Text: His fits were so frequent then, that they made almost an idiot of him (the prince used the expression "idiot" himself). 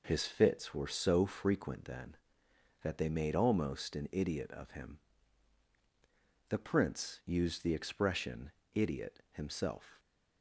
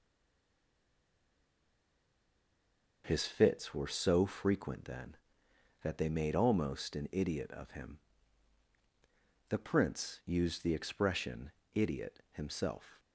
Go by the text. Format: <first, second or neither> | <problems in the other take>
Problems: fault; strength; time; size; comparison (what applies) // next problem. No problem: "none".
first | stays silent before the first word; strong; until 3.0 s; 3.0 s long // pauses between "expression" and "idiot"; slight; at 11.5 s; 0.24 s long; slight in the first